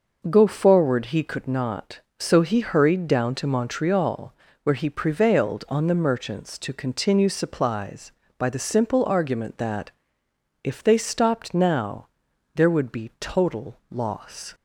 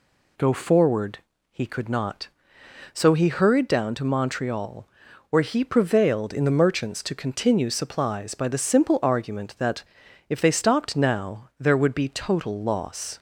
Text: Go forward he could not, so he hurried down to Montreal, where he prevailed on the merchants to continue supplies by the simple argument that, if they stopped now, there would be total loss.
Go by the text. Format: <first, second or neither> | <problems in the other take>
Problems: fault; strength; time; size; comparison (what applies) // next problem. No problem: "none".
first | pauses between "forward" and "he"; slight; at 1.1 s; 0.32 s long // says "in" for "on"; at 6.3 s